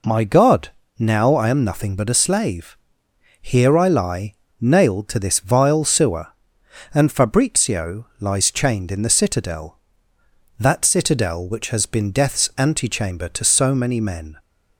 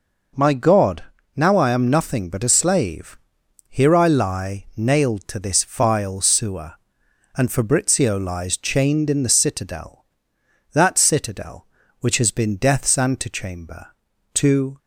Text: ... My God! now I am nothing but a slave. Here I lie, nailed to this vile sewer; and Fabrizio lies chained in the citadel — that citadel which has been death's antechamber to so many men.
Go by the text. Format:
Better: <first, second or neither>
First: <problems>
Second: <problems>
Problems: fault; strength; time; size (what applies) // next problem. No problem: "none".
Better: first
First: none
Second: stops before "so many men"; at 14.7 s